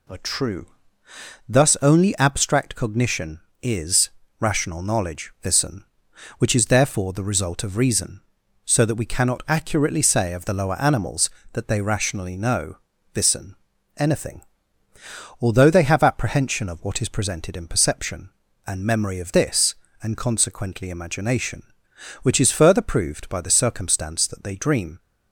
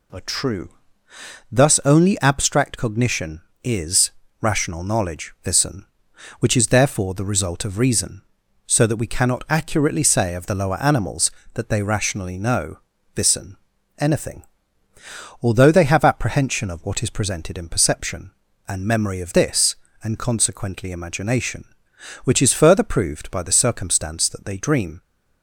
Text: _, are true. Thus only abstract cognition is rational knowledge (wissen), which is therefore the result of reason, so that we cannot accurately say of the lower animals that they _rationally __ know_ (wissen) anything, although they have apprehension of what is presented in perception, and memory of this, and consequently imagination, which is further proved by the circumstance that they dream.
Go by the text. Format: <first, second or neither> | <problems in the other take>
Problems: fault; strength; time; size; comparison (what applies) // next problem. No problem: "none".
neither | pauses between "is" and "rational"; slight; the same in both